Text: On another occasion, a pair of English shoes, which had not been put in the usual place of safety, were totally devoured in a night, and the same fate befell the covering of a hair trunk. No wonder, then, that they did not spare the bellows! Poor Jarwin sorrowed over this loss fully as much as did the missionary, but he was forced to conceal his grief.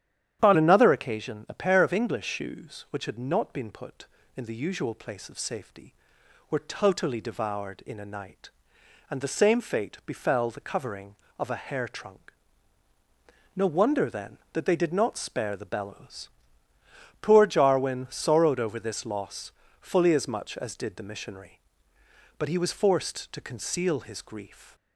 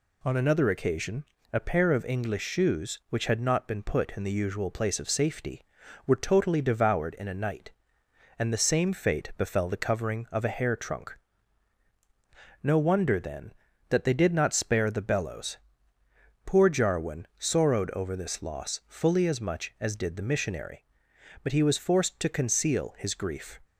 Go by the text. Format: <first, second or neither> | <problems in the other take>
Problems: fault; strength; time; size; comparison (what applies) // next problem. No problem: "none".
second | starts louder than the rest; strong; until 1.4 s; 10.5 dB // changes voice at "another"; from 0.5 s on; 24.2 s long // pauses between "loss" and "fully"; slight; at 19.5 s; 0.28 s long